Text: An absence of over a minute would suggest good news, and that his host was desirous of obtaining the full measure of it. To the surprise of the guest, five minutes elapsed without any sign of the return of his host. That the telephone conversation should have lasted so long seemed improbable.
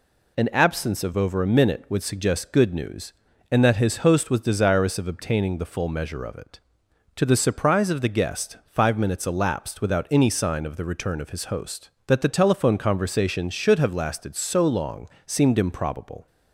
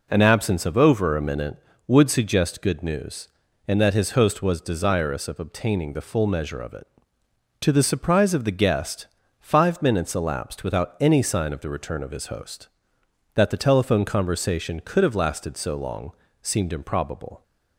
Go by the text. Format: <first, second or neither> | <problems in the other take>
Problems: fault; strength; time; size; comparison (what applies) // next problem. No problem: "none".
first | says "could" for "should"; at 14.8 s // pauses between "long" and "seemed"; slight; at 16.1 s; 0.28 s long; slight in the first